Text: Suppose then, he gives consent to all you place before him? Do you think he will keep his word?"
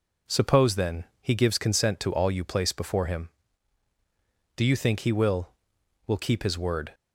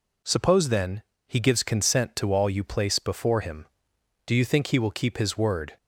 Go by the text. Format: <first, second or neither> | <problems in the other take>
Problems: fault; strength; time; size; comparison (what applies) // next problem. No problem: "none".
second | says "will" twice; at 6.0 s